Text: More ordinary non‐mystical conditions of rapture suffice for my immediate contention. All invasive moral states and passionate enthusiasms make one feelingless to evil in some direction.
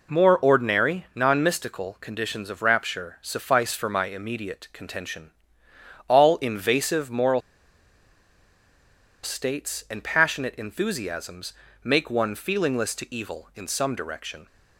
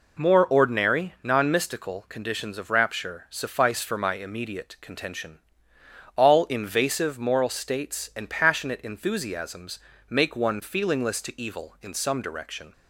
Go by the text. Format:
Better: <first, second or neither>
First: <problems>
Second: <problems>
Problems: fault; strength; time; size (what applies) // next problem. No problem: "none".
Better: second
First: pauses between "moral" and "states"; strong; at 7.4 s; 1.8 s long // pauses between "enthusiasms" and "make"; slight; at 11.5 s; 0.32 s long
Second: pauses between "enthusiasms" and "make"; slight; at 9.7 s; 0.32 s long